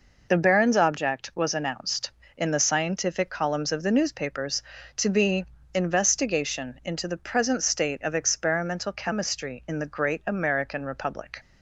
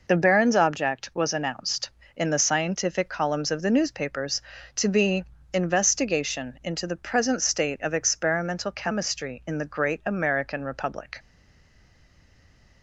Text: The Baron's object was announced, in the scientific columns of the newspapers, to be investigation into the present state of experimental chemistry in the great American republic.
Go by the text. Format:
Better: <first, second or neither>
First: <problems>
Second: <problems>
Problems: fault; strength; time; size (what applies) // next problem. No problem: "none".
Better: first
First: pauses between "be" and "investigation"; slight; at 5.4 s; 0.28 s long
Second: pauses between "be" and "investigation"; slight; at 5.2 s; 0.28 s long // stays silent after the last word; noticeable; from 11.1 s on; 1.7 s long